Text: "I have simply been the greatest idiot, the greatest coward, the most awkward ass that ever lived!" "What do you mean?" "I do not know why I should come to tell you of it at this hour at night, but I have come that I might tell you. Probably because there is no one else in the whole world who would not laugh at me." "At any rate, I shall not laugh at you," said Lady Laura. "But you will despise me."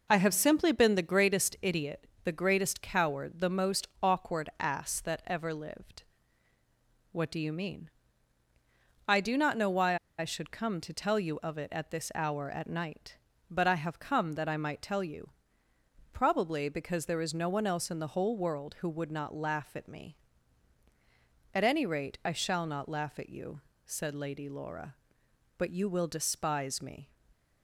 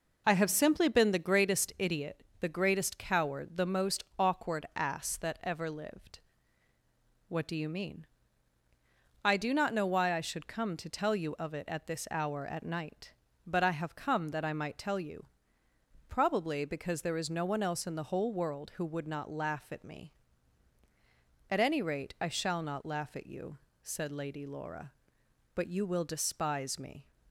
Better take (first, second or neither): second